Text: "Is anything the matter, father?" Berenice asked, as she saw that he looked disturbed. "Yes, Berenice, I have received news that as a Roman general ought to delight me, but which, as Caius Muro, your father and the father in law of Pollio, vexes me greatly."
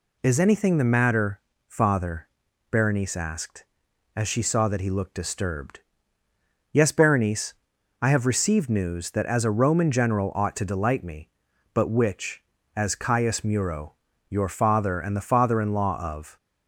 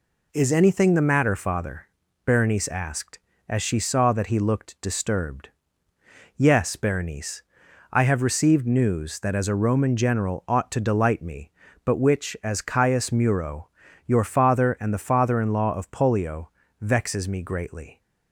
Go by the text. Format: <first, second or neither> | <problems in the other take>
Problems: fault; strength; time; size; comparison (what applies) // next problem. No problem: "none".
second | stops before "Pollio vexes me greatly"; at 16.3 s